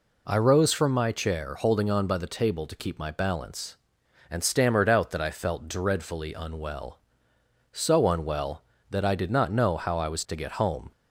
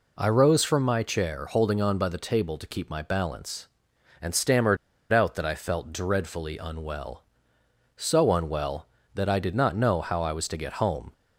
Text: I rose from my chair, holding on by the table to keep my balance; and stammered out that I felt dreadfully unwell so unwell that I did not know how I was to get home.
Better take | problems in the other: first | pauses between "stammered" and "out"; slight; at 4.7 s; 0.35 s long

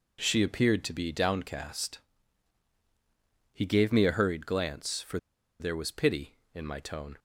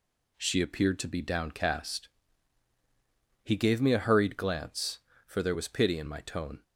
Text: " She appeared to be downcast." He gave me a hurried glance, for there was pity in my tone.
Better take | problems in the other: second | pauses between "for" and "there"; at 5.1 s; 0.42 s long

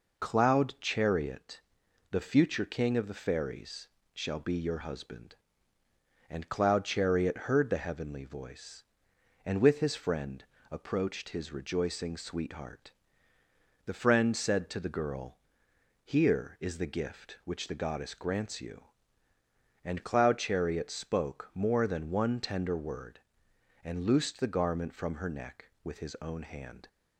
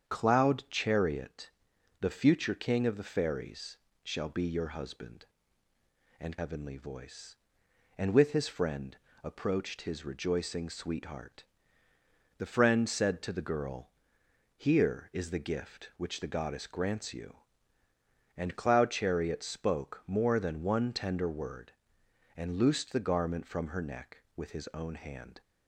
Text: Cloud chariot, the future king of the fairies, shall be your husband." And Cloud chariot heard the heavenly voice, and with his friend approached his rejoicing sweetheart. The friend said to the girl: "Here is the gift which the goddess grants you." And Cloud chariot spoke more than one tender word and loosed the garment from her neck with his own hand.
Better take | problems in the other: first | starts louder than the rest; strong; until 1.1 s; 7.5 dB // skips "Cloud chariot heard the"; at 6.3 s // pauses between "friend" and "approached"; slight; at 8.9 s; 0.26 s long; slight in the first

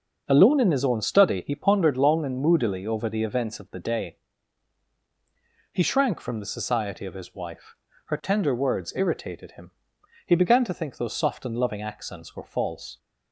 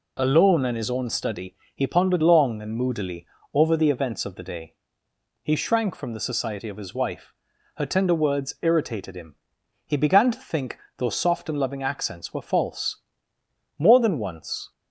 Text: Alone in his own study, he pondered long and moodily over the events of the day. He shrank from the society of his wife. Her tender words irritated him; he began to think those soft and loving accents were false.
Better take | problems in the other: first | pauses between "moodily" and "over"; slight; at 3.2 s; 0.26 s long // pauses between "think" and "those"; slight; at 10.7 s; 0.18 s long // goes on to say "More than once"; noticeable; from 13.7 s on; 0.94 s long

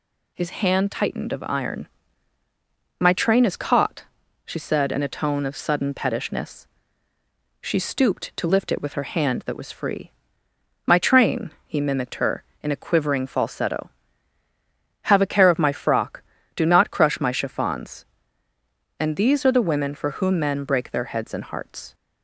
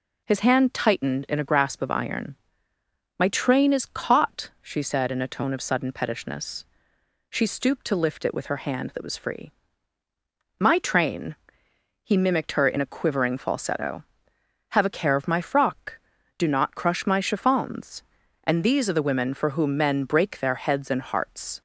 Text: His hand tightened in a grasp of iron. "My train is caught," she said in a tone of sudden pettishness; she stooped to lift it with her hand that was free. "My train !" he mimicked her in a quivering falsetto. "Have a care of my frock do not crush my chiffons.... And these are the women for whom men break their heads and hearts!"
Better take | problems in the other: second | skips "in a grasp"; at 1.3 s

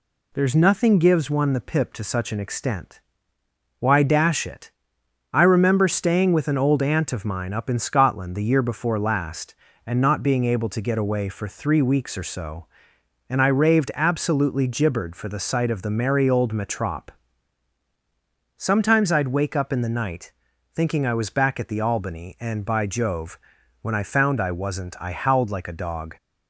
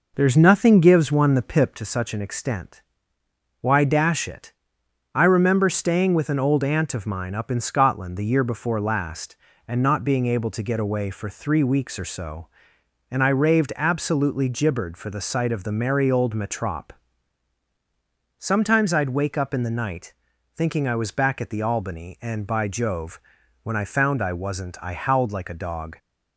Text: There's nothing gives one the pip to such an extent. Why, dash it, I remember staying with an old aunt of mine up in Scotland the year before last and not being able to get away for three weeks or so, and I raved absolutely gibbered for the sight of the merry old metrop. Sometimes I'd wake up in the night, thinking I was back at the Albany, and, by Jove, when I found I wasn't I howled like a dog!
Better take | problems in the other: first | starts louder than the rest; noticeable; until 1.8 s; 5 dB

